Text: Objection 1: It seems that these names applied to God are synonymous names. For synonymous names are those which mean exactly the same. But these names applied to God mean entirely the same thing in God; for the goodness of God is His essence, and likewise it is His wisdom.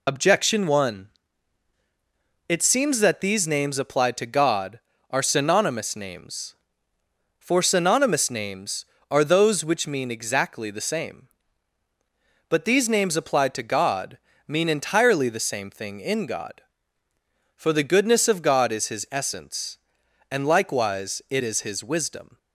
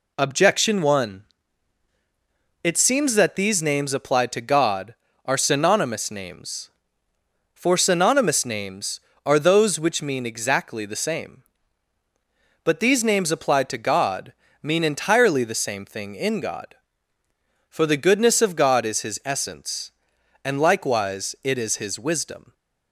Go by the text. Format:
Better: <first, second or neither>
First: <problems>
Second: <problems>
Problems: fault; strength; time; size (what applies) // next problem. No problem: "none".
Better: second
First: loses the start of "Objection"; at 0.0 s; 60 ms // pauses between "God" and "mean"; slight; at 14.1 s; 0.30 s long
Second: pauses between "God" and "mean"; slight; at 14.3 s; 0.30 s long